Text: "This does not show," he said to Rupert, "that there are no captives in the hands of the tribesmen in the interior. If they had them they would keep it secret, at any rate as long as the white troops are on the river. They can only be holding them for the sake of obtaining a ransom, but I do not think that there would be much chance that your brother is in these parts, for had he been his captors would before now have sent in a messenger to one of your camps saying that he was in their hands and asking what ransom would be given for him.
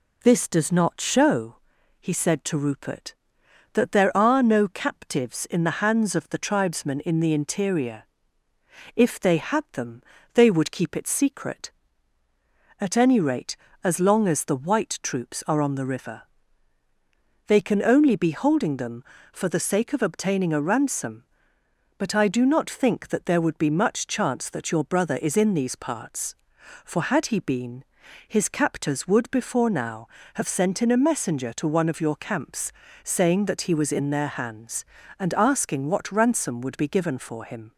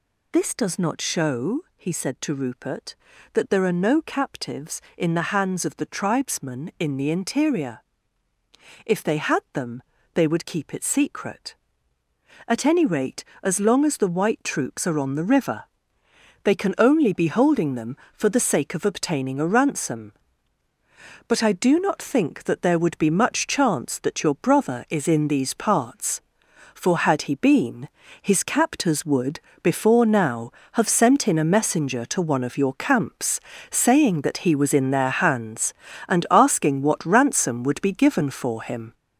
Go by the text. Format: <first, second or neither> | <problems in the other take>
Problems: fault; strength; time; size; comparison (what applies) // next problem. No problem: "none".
first | gets louder; noticeable; throughout; 6 dB // pauses between "them" and "they"; slight; at 9.8 s; 0.34 s long; slight in the first // pauses between "been" and "his"; slight; at 27.8 s; 0.34 s long; also in the first // pauses between "would" and "before"; slight; at 29.3 s; 0.22 s long // pauses between "camps" and "saying"; slight; at 33.3 s; 0.30 s long; slight in the first